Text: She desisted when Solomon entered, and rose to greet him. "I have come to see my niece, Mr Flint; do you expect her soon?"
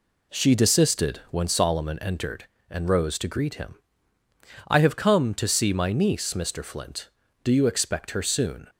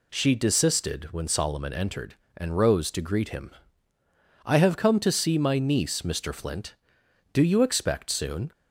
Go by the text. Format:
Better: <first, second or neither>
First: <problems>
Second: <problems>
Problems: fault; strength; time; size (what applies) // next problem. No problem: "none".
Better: first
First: none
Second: skips "her"; at 8.1 s